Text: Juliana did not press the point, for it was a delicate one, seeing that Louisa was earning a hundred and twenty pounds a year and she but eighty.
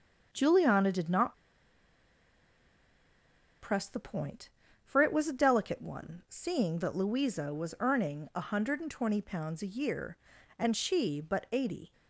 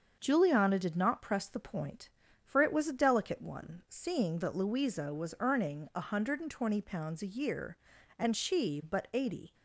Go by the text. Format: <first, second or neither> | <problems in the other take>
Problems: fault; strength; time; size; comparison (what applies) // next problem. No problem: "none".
second | starts louder than the rest; until 1.3 s; 7 dB; also in the second // pauses between "not" and "press"; strong; at 1.3 s; 2.2 s long